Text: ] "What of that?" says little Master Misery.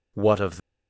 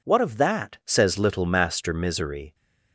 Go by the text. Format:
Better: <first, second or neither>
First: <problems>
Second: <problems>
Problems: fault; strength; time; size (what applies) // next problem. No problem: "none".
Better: second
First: stops before "that says little Master Misery"; at 0.5 s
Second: none